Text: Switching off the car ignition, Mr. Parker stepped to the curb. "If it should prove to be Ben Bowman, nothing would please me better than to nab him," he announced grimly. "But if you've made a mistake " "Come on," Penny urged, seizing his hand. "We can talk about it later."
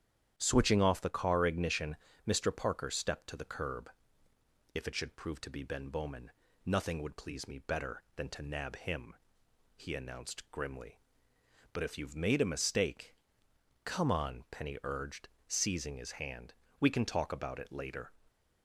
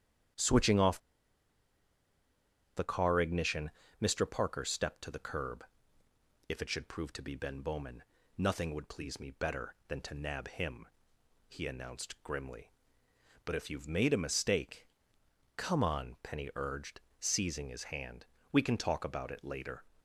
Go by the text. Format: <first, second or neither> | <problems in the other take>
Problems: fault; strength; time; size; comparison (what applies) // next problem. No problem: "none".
first | starts louder than the rest; strong; until 3.1 s; 10 dB; strong in the first // pauses between "off" and "the"; strong; at 0.9 s; 1.7 s long